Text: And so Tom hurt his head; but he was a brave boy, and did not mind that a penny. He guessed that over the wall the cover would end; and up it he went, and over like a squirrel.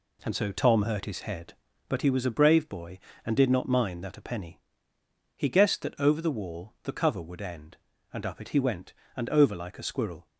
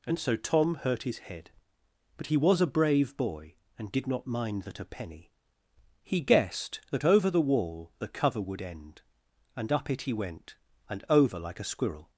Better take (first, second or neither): neither